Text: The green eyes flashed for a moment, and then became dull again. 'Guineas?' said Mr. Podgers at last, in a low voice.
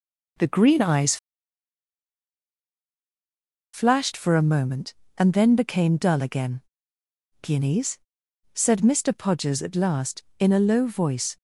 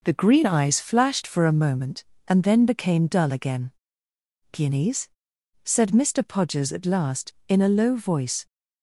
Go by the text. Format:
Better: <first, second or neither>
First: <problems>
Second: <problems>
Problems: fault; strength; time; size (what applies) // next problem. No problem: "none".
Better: second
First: pauses between "eyes" and "flashed"; strong; at 1.1 s; 2.5 s long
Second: none